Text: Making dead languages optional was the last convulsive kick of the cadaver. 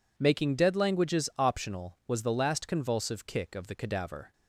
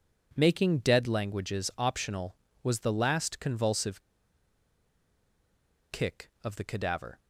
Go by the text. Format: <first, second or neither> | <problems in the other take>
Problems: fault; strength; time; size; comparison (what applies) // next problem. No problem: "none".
first | pauses between "convulsive" and "kick"; strong; at 4.0 s; 1.8 s long